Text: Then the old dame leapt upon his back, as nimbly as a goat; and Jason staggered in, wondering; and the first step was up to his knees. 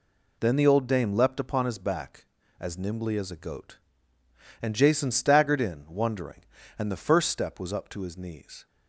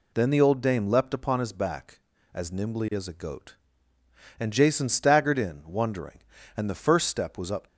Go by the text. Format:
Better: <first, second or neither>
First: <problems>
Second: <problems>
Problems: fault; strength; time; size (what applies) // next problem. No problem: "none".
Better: first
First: none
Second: stops before "to his knees"; at 7.6 s